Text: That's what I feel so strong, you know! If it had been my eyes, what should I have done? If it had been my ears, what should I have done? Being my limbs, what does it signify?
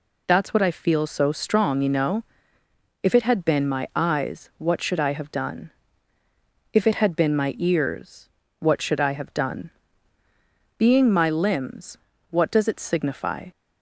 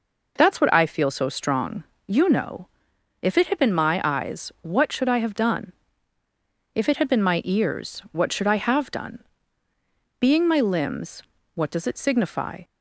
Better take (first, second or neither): neither